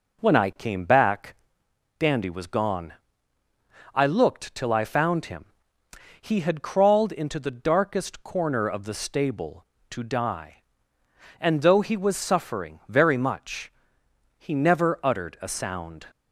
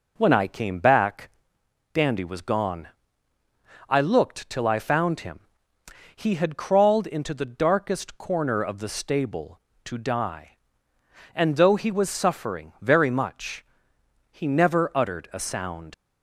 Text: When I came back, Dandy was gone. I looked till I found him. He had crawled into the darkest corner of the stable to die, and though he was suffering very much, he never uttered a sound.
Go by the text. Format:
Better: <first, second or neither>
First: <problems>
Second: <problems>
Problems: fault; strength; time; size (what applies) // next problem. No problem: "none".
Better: first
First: none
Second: leaves "sound" unfinished; at 15.9 s; 70 ms